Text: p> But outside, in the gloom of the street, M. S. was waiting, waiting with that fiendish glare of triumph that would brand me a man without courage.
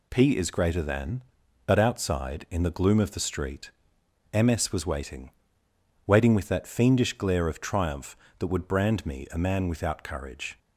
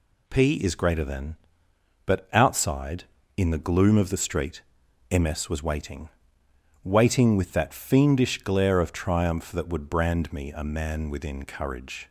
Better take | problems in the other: first | says "within" for "without"; at 11.1 s

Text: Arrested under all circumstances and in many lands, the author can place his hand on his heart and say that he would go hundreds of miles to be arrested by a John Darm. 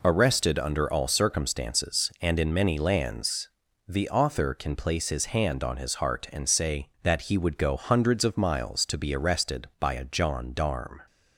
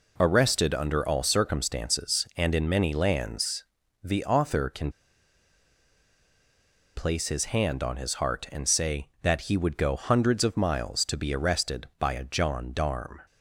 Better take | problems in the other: first | pauses between "can" and "place"; strong; at 4.9 s; 2.0 s long

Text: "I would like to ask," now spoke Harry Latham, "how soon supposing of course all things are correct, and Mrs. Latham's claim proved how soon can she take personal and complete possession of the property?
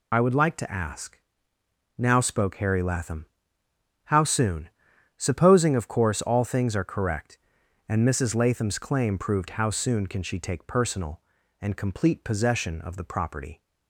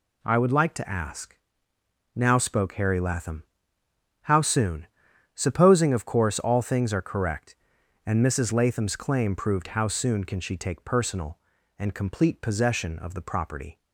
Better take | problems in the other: second | loses the start of "I"; at 0.1 s; 65 ms // pauses between "soon" and "supposing"; noticeable; at 4.6 s; 0.48 s long; noticeable in the second

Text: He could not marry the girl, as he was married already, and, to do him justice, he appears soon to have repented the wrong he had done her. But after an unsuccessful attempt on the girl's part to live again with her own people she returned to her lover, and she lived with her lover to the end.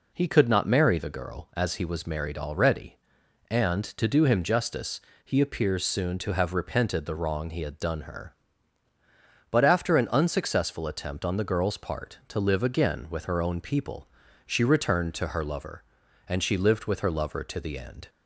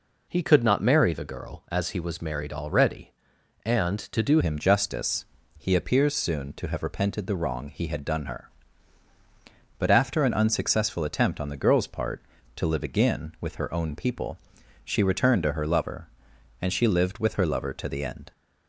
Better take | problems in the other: first | changes voice at "him"; from 4.4 s on; 13.9 s long // pauses between "people" and "she"; noticeable; at 14.3 s; 0.46 s long; also in the first

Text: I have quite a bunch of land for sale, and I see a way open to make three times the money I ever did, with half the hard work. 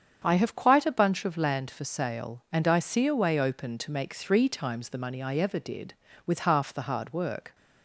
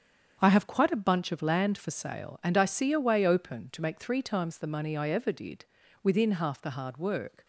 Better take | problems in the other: first | starts louder than the rest; strong; until 1.4 s; 7.5 dB; strong in the first // says "within" for "with"; at 6.0 s

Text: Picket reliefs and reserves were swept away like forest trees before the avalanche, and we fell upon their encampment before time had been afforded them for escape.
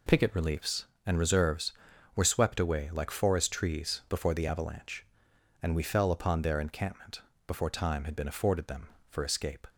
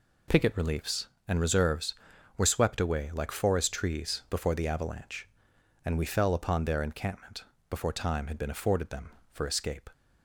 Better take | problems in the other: neither | pauses between "encampment" and "before"; slight; the same in both

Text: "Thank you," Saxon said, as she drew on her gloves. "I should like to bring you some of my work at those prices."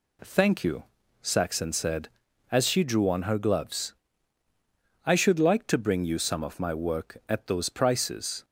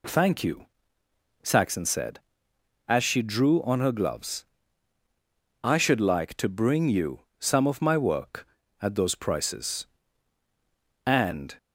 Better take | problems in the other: first | pauses between "you" and "some"; slight; at 7.2 s; 0.18 s long // goes on to say "And"; from 11.0 s on; 0.50 s long

